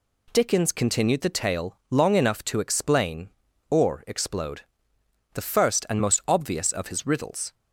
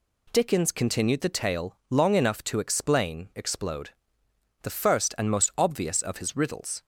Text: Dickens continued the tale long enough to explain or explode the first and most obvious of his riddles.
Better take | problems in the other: first | skips "or"; at 3.3 s // pauses between "explode" and "the"; noticeable; at 3.8 s; 0.72 s long; noticeable in the first

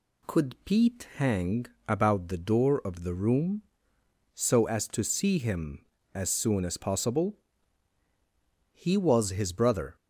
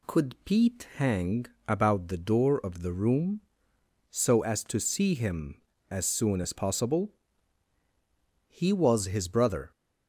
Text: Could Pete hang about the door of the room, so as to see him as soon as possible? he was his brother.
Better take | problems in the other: neither | pauses between "hang" and "about"; slight; the same in both

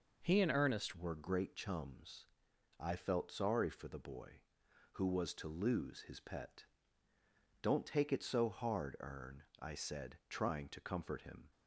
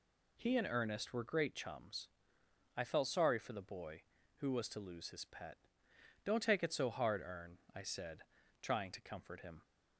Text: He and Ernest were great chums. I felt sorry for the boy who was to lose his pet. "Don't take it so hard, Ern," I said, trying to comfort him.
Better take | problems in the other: second | changes voice at "were"; from 0.9 s on; 10.5 s long

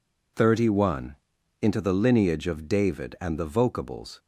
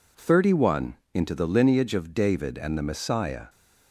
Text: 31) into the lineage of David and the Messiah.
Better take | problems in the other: second | says "Vocables" for "Messiah"; at 3.4 s

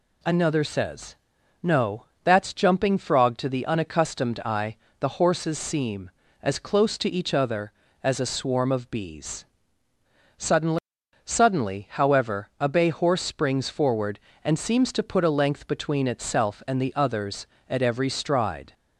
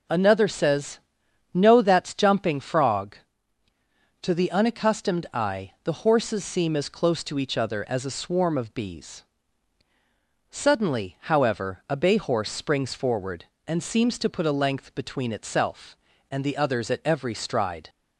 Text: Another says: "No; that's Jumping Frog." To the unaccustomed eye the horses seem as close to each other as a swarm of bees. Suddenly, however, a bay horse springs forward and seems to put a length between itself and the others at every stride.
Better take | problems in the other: second | pauses between "eye" and "the"; slight; at 4.7 s; 0.24 s long // says "Suddenly" twice; at 11.2 s

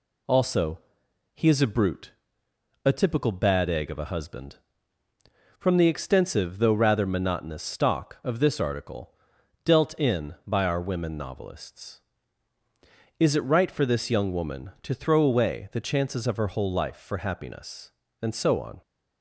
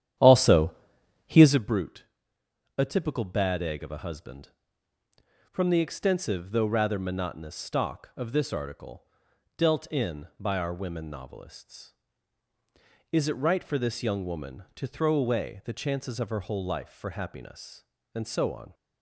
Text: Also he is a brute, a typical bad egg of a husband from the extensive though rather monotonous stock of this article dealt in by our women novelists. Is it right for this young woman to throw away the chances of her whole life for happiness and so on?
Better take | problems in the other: first | starts louder than the rest; strong; until 1.6 s; 10.5 dB // pauses between "Also" and "he"; noticeable; at 0.7 s; 0.54 s long; noticeable in the first // pauses between "article" and "dealt"; noticeable; at 9.0 s; 0.52 s long; noticeable in the first

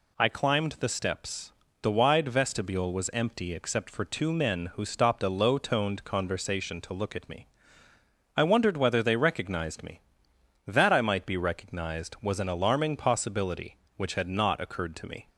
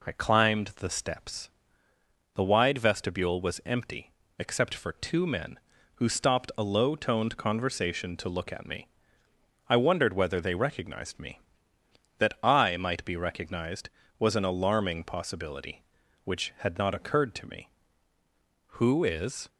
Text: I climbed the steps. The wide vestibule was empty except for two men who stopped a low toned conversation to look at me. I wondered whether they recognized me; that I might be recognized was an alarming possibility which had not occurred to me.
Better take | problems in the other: first | pauses between "empty" and "except"; slight; at 4.1 s; 0.28 s long // goes on to say "Who is"; noticeable; from 18.7 s on; 0.70 s long

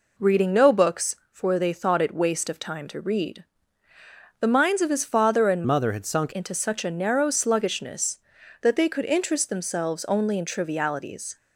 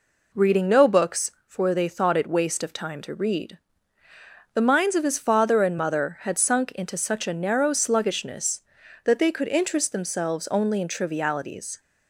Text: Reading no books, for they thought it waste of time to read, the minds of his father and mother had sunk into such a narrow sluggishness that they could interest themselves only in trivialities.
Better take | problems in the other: second | changes voice from "mother" to "sunk"; from 5.6 to 6.3 s; 0.7 s long

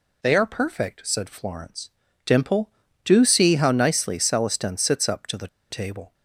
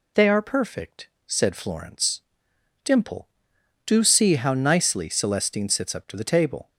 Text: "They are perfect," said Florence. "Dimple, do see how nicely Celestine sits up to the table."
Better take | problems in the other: second | pauses between "the" and "table"; slight; at 5.4 s; 0.23 s long

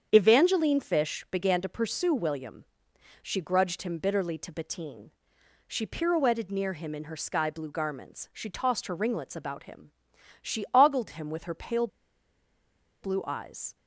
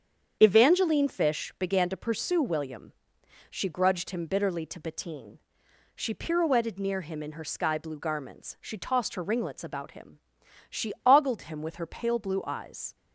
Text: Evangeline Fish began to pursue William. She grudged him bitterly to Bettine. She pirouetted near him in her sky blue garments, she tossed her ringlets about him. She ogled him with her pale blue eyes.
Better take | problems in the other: second | starts louder than the rest; strong; until 1.1 s; 8 dB; strong in the second // pauses between "pale" and "blue"; at 11.8 s; 1.1 s long

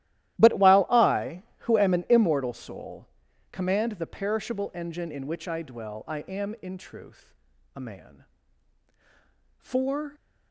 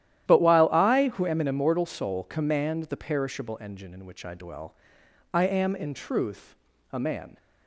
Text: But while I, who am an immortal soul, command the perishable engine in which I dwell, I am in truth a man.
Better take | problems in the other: second | starts louder than the rest; strong; until 1.4 s; 14 dB; strong in the second // pauses between "truth" and "a"; at 7.3 s; 0.42 s long; slight in the second // goes on to say "For"; from 9.5 s on; 0.58 s long

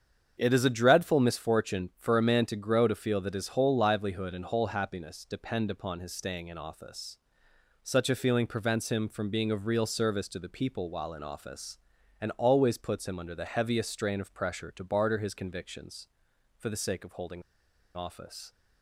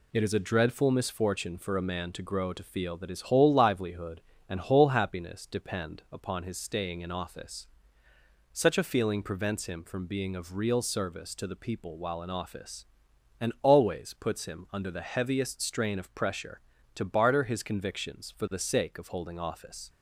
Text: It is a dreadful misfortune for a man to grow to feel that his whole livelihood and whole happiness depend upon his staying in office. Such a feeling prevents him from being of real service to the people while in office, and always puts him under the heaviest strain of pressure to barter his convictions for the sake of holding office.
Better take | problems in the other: second | starts louder than the rest; strong; until 1.3 s; 7.5 dB // pauses between "holding" and "office"; noticeable; at 17.4 s; 0.52 s long

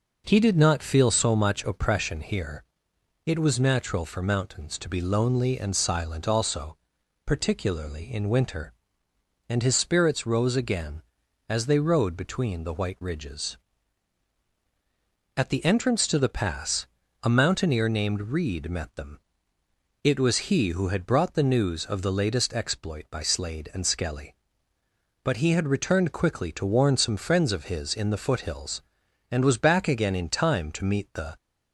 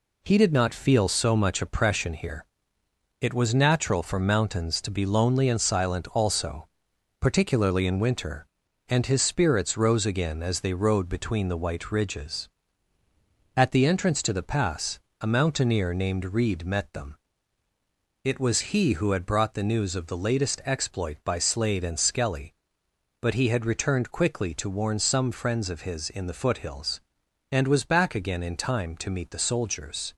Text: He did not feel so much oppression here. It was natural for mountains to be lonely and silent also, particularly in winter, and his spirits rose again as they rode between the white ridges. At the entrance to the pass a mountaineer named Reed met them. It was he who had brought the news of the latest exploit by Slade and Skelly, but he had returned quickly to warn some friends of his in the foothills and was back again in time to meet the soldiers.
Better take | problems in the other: second | pauses between "pass" and "a"; slight; at 16.8 s; 0.34 s long; slight in the second // stops before "soldiers"; at 31.3 s

